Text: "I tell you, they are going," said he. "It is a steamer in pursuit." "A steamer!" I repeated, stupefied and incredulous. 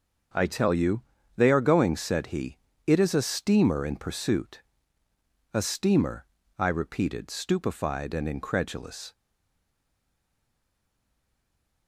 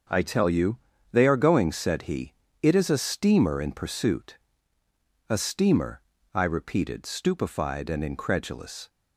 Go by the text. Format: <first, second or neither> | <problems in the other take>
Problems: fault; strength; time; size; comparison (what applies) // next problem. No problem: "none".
second | starts louder than the rest; until 1.6 s; 6 dB; noticeable in the second // stays silent after the last word; strong; from 9.1 s on; 2.7 s long